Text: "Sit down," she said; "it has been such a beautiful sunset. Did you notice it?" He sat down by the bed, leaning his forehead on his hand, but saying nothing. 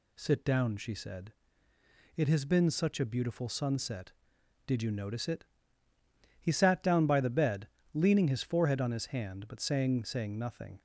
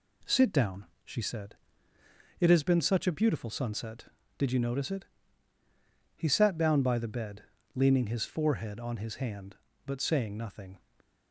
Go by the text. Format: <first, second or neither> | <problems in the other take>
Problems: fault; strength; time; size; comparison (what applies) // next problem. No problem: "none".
second | says "saying" twice; at 10.0 s